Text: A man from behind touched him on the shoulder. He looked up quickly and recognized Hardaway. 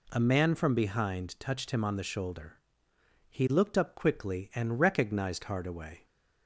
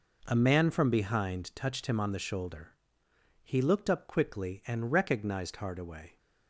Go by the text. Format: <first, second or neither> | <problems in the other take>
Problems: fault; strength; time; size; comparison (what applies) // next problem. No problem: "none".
first | gets quieter; strong; throughout; 12 dB